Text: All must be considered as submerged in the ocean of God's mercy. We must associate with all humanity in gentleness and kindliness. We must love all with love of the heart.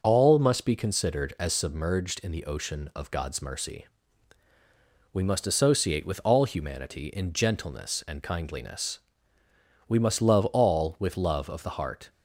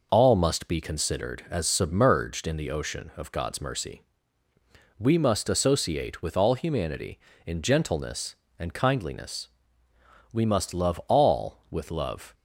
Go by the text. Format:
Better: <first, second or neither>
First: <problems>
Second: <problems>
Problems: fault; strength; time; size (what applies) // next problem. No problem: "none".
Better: first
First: none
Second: stops before "of the heart"; at 12.3 s